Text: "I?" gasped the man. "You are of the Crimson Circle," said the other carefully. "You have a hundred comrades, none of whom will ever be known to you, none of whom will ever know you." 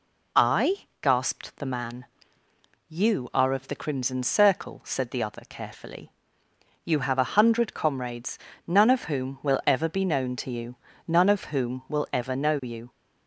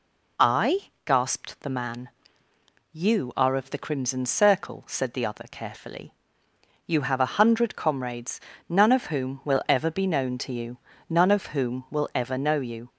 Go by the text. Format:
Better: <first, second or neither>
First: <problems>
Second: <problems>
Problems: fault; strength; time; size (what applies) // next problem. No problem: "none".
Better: neither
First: none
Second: none